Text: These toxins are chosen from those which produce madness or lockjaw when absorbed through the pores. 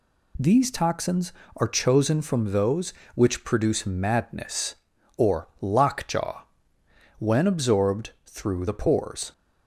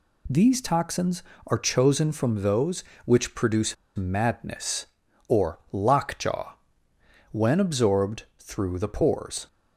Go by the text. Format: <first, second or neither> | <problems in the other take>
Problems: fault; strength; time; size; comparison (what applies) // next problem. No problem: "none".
first | pauses between "produce" and "madness"; slight; at 3.7 s; 0.21 s long // pauses between "lockjaw" and "when"; noticeable; at 6.5 s; 0.76 s long; noticeable in the first // pauses between "absorbed" and "through"; slight; at 8.2 s; 0.16 s long; slight in the first